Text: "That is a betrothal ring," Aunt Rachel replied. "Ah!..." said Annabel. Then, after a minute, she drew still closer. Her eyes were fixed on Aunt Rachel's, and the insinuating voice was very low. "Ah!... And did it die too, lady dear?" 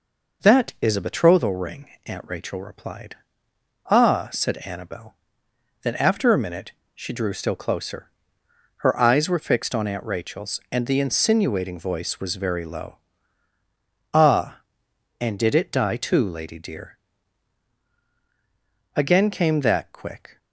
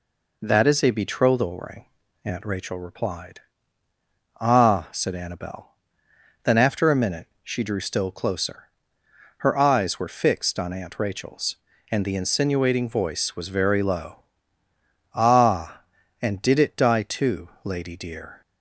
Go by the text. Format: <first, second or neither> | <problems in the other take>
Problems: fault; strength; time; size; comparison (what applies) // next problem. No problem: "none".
second | goes on to say "Again came that quick"; from 18.9 s on; 1.4 s long